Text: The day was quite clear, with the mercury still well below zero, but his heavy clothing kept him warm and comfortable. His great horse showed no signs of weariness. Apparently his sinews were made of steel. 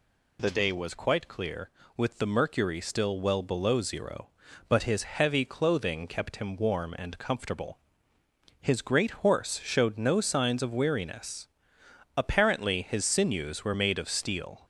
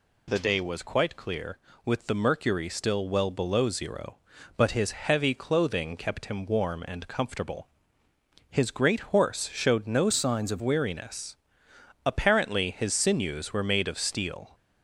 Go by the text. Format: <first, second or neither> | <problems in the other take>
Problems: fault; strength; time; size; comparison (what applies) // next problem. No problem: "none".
first | changes voice from "signs" to "of"; from 10.1 to 10.6 s; 0.5 s long